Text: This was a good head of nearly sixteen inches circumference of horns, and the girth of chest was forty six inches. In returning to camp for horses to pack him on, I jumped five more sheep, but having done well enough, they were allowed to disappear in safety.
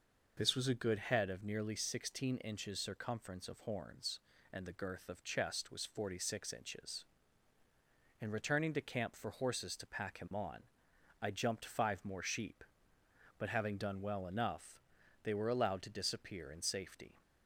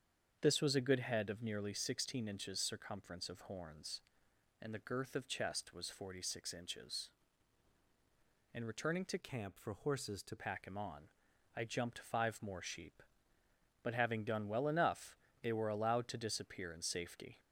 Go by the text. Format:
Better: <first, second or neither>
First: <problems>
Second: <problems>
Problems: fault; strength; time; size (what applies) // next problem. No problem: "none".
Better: first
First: none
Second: starts louder than the rest; strong; until 1.4 s; 7.5 dB // changes voice from "camp" to "to"; from 9.1 to 10.3 s; 1.2 s long